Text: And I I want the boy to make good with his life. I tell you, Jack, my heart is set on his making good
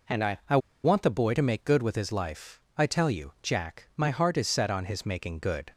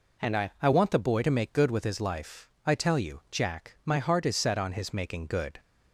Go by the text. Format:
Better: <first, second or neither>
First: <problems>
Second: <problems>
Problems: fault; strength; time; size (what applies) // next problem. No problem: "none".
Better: second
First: pauses between "I" and "want"; slight; at 0.5 s; 0.26 s long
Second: none